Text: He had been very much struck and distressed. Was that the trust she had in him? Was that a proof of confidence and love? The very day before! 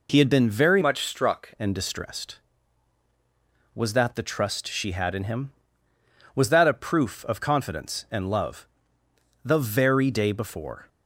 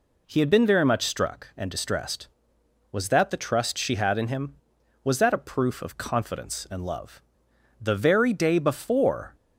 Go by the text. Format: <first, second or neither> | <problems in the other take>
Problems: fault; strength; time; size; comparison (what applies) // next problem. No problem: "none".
second | changes voice from "much" to "struck"; from 0.8 to 1.5 s; 0.7 s long